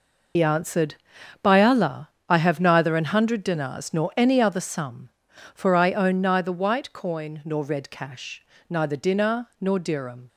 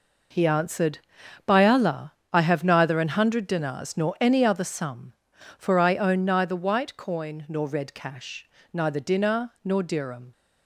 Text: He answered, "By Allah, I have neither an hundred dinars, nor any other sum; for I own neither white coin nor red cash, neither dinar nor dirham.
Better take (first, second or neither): second